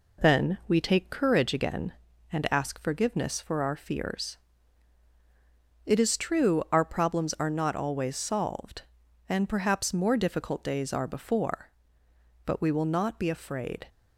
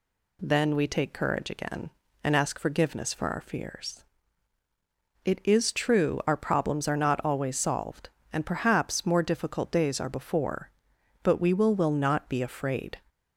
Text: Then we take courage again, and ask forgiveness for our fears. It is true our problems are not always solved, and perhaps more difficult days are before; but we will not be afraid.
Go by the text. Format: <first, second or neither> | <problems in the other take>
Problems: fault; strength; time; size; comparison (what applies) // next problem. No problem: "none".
first | says "will" twice; at 11.7 s